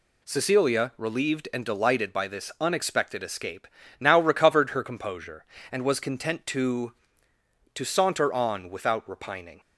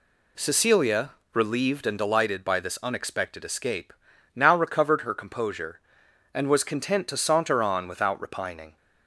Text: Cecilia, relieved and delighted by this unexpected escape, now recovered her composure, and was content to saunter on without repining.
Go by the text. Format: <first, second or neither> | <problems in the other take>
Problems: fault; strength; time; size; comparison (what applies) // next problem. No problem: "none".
second | says "to" twice; at 7.7 s